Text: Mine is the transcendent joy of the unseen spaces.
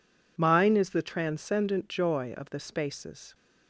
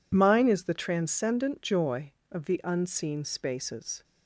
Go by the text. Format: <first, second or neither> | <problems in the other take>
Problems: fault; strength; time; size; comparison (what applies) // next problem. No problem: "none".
second | skips "unseen"; at 2.6 s